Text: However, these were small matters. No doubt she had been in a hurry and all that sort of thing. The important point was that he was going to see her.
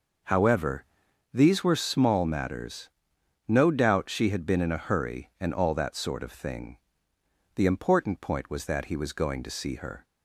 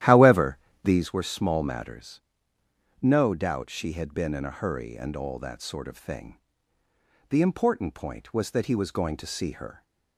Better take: first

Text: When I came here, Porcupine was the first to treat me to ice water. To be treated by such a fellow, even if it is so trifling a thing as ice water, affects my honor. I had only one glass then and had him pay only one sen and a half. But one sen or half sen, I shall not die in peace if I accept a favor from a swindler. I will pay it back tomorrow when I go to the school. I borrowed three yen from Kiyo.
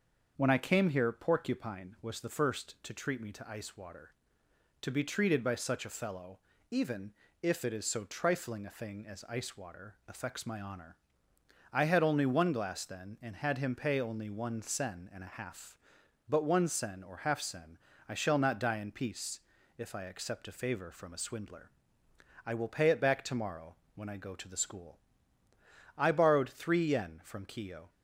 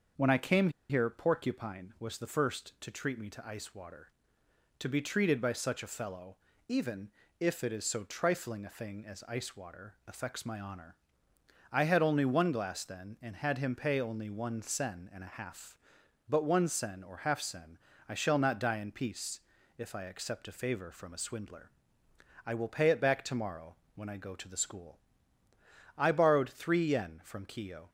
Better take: first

